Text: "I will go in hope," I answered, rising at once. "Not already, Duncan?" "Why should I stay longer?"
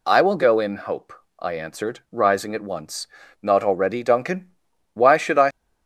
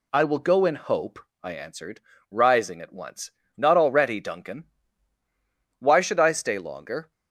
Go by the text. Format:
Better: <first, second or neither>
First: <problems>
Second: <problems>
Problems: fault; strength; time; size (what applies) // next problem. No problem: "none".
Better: second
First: stops before "stay longer"; at 5.5 s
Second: none